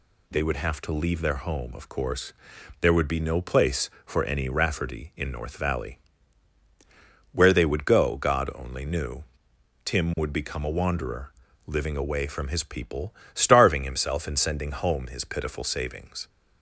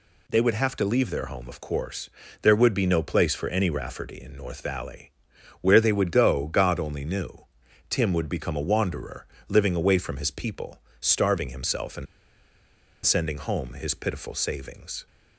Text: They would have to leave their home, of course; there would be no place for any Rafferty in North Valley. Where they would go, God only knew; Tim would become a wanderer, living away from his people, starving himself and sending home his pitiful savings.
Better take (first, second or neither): first